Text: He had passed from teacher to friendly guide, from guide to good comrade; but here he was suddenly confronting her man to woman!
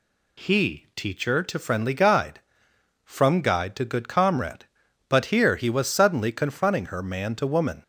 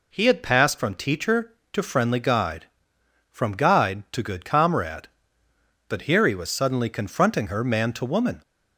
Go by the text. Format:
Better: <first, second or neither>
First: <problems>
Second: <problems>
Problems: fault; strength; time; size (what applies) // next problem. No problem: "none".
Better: second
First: skips "had passed from"; at 0.9 s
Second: none